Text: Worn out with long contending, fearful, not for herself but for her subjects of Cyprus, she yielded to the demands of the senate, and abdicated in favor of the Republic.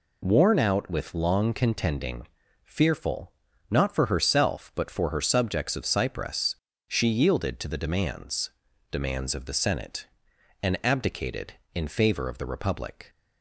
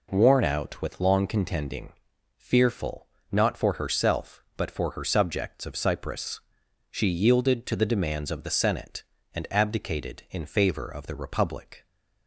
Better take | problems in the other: second | says "demands" twice; at 8.8 s

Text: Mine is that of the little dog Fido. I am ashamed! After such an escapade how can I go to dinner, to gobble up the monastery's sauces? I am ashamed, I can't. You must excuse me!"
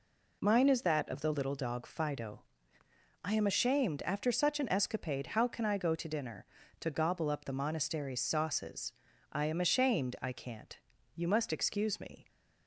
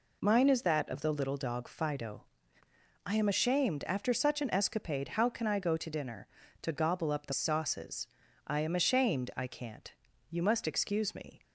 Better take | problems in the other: first | skips "monastery's"; at 7.3 s

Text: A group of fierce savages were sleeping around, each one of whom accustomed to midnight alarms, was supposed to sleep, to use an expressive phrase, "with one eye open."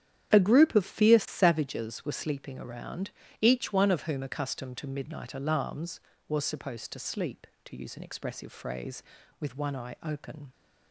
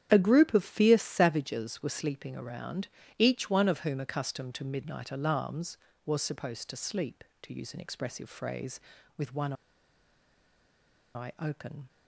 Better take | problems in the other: first | starts louder than the rest; strong; until 1.1 s; 9.5 dB; strong in the first // pauses between "one" and "eye"; strong; at 9.5 s; 1.6 s long

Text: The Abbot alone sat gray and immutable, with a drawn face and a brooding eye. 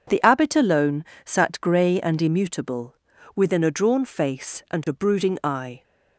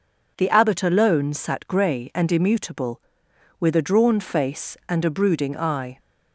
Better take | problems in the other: second | pauses between "alone" and "sat"; slight; at 1.0 s; 0.22 s long // says "within" for "with"; at 3.3 s

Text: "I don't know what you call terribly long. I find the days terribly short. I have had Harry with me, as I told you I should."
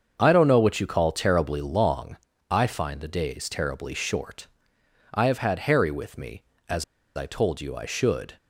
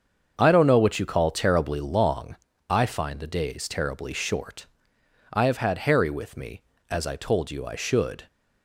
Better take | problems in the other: second | starts louder than the rest; until 1.2 s; 7 dB; also in the second // pauses between "as" and "I"; slight; at 6.8 s; 0.32 s long

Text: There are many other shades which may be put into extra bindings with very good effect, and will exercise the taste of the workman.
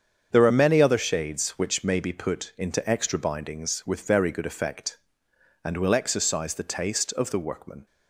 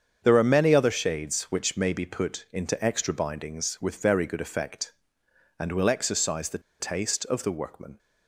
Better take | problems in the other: first | starts louder than the rest; strong; until 1.2 s; 7.5 dB; strong in the first // pauses between "the" and "taste"; slight; at 6.6 s; 0.20 s long

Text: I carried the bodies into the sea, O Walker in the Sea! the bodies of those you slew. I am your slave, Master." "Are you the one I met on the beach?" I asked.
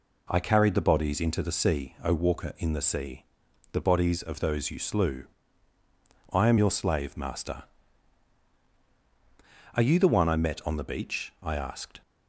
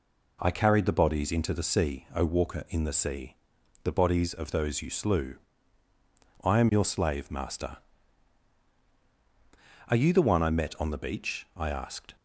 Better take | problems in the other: neither | none

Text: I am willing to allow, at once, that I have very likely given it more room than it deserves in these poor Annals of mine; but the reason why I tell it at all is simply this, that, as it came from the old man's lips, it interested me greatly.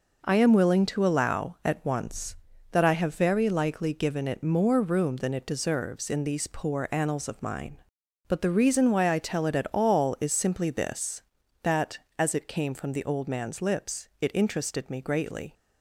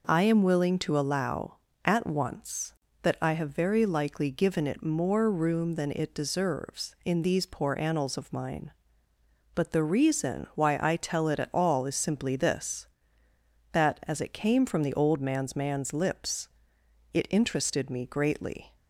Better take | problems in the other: first | says "man's" twice; at 15.5 s

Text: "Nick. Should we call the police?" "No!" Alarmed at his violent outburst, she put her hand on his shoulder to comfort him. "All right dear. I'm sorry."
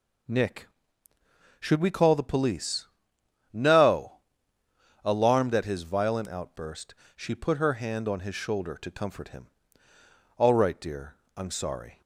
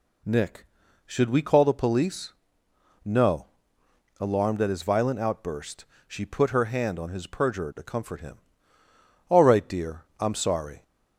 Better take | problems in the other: first | says "perjurer" for "shoulder"; at 7.2 s

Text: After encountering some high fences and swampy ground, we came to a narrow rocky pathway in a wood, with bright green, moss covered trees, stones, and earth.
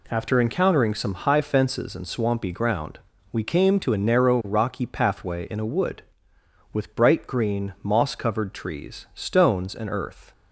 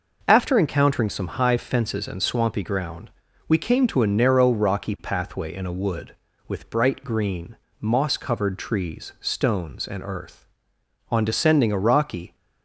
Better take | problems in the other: first | goes on to say "On descending a rocky"; noticeable; from 11.1 s on; 1.2 s long

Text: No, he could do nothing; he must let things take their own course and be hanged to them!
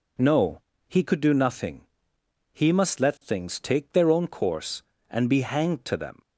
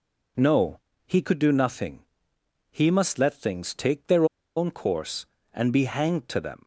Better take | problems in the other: first | pauses between "their" and "own"; slight; at 4.2 s; 0.31 s long

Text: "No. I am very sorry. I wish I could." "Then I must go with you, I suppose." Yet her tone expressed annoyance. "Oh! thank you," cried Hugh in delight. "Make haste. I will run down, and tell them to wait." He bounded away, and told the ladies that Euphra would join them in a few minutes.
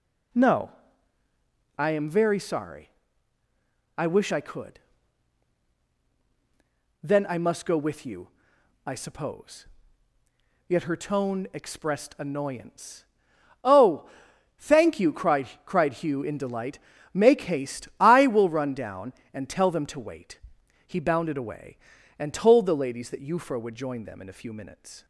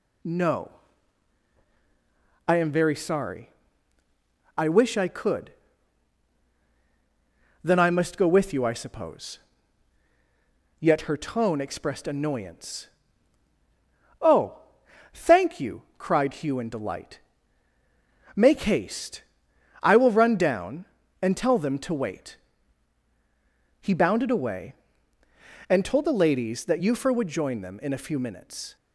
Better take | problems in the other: second | says "cried" twice; at 15.6 s

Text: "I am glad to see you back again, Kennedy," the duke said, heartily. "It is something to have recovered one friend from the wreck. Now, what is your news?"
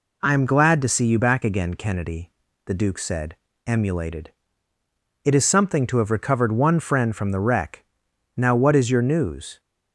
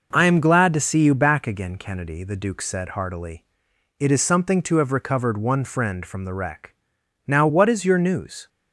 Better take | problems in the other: second | says "emulated" for "heartily"; at 3.6 s

